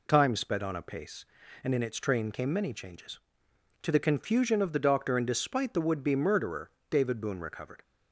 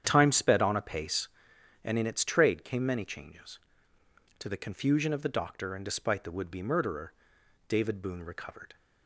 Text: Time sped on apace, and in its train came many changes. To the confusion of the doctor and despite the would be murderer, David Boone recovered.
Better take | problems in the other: first | starts louder than the rest; strong; until 1.0 s; 9 dB // says "trade" for "train"; at 2.2 s

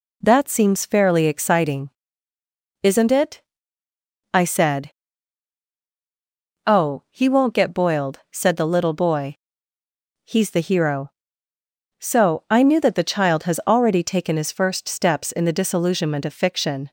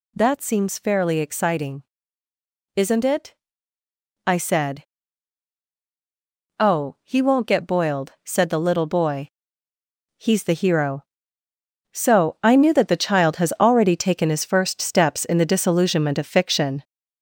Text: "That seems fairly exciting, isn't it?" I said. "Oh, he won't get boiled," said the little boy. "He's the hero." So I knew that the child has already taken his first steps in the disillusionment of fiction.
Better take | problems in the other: first | gets louder; noticeable; throughout; 4 dB

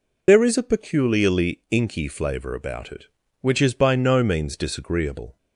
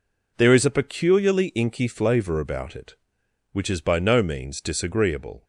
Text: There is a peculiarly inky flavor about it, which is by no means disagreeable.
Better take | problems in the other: second | loses the start of "There"; at 0.2 s; 65 ms

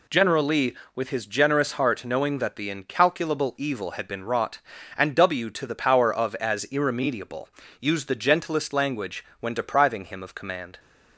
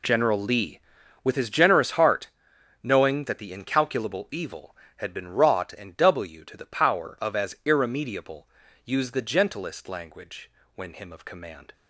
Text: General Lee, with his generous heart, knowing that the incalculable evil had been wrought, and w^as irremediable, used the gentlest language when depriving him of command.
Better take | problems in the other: first | pauses between "language" and "when"; slight; at 10.5 s; 0.24 s long; slight in the first // skips "depriving"; at 10.9 s

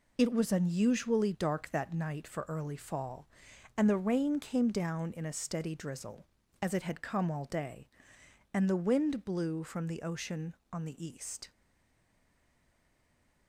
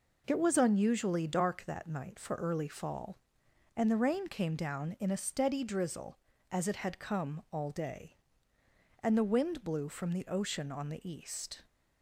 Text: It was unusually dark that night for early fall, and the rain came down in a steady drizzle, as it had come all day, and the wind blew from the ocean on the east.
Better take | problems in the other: second | stays silent after the last word; noticeable; from 11.5 s on; 1.9 s long

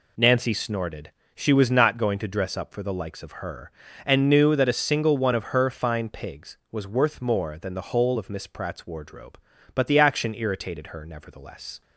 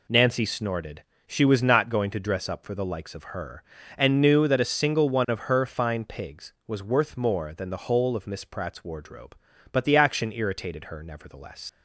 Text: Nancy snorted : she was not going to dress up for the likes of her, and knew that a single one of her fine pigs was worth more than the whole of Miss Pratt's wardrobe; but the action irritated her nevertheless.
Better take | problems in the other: first | leaves "nevertheless" unfinished; at 11.6 s; 90 ms

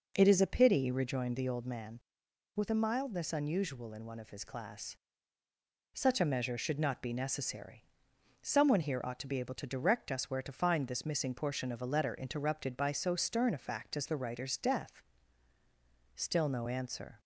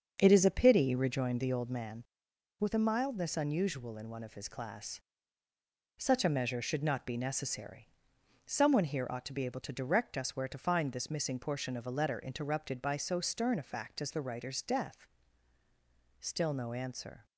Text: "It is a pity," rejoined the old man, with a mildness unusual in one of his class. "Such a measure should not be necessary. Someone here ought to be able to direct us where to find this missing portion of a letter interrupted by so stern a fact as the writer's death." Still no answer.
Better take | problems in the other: first | gets quieter; throughout; 7 dB

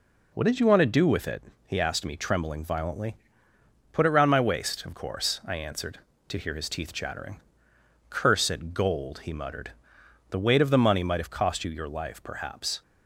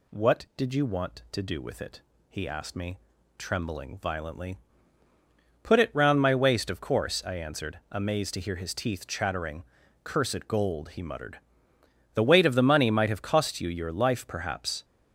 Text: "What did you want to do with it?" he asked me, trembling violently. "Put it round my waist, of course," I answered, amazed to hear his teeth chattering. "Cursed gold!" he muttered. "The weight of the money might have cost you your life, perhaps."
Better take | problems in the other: second | skips "amazed"; at 6.1 s

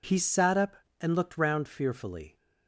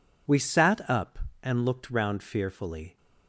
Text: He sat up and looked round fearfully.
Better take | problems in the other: first | says "We" for "He"; at 0.2 s

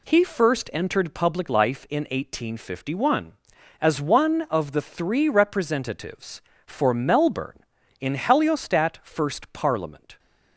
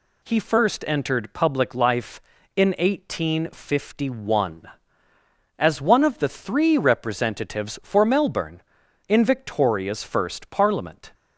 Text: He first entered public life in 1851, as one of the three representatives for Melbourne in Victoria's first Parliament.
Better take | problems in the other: second | says "Heliostat" for "Victoria's"; at 8.1 s

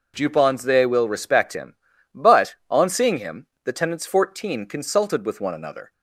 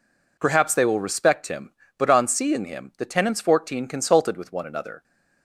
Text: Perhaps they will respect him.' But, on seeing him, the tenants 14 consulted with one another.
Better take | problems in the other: second | says "Jupons" for "Perhaps"; at 0.1 s

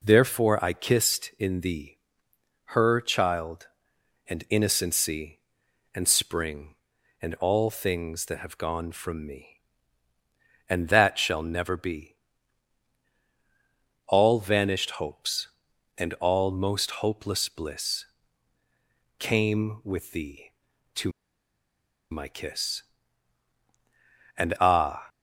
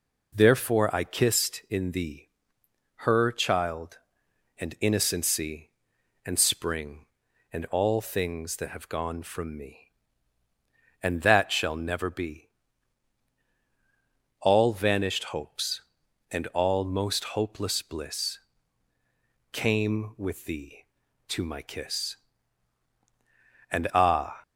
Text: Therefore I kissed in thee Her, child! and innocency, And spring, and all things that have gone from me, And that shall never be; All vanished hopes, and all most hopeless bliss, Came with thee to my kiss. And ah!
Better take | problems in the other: second | pauses between "thee" and "Her"; noticeable; at 1.9 s; 0.68 s long; noticeable in the second // pauses between "to" and "my"; at 21.1 s; 1.0 s long

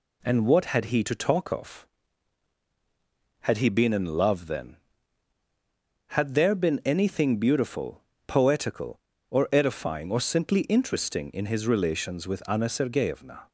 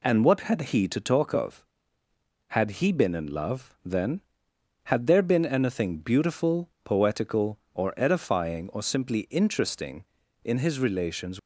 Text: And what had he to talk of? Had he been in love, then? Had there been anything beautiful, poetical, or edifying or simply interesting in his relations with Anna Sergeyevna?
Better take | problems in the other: first | stops before "with Anna Sergeyevna"; at 11.3 s

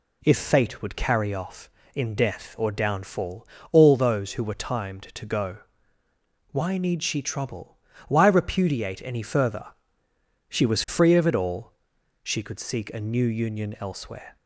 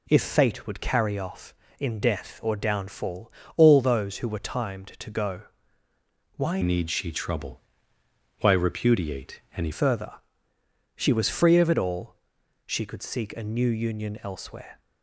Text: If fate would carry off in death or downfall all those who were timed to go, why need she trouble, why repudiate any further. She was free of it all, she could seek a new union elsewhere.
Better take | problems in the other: first | pauses between "downfall" and "all"; slight; at 3.3 s; 0.26 s long; slight in the first // changes voice from "need" to "any"; from 6.6 to 9.7 s; 3.1 s long // pauses between "repudiate" and "any"; slight; at 9.3 s; 0.18 s long

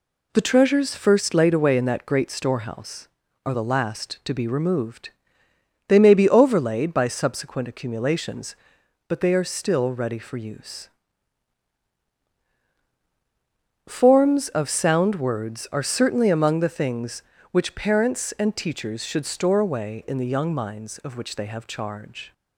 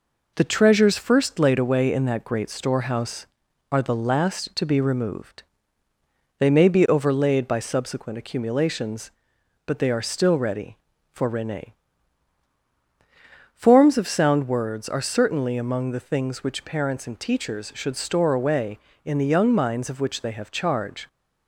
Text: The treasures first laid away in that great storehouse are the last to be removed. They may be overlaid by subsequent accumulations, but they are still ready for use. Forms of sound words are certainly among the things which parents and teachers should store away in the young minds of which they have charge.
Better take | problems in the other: first | says "rene" for "use"; at 11.2 s

